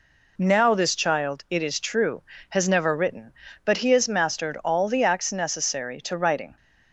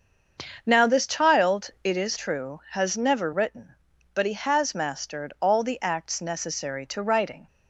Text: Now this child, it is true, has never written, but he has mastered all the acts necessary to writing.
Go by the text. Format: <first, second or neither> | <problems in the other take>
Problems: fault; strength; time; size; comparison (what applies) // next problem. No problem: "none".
first | starts louder than the rest; until 2.3 s; 6.5 dB